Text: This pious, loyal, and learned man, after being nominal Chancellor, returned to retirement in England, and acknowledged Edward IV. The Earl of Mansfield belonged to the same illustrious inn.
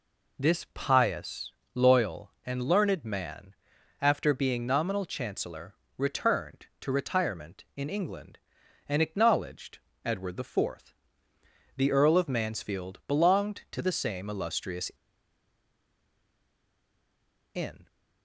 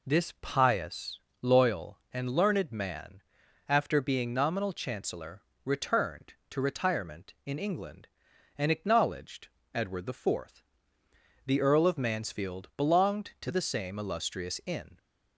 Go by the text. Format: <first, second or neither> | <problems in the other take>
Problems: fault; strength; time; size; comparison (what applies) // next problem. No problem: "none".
second | pauses between "acknowledged" and "Edward"; slight; at 9.7 s; 0.26 s long; slight in the second // pauses between "illustrious" and "inn"; strong; at 14.9 s; 2.6 s long